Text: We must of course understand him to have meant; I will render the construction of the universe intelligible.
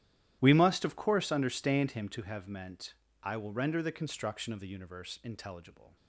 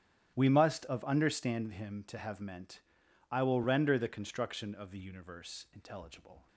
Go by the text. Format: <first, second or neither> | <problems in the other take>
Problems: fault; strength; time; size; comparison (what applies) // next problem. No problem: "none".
first | starts louder than the rest; strong; until 1.3 s; 12 dB; strong in the first // skips "course"; at 1.0 s